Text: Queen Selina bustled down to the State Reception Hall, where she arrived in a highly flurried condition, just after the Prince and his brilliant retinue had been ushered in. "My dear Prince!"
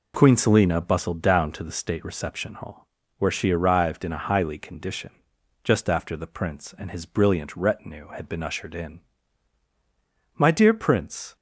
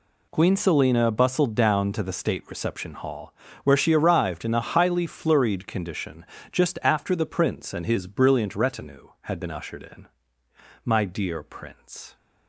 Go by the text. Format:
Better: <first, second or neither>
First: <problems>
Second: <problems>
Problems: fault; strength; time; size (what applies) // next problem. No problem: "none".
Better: second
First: skips "flurried"; at 4.5 s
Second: none